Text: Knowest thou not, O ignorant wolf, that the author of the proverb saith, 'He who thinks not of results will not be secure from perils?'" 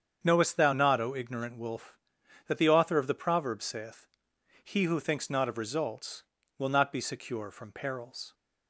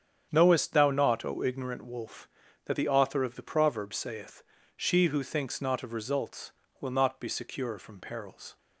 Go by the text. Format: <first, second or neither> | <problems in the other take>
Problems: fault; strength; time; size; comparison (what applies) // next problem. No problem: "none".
first | starts louder than the rest; strong; until 1.3 s; 8.5 dB; strong in the first // says "She" for "He"; at 4.7 s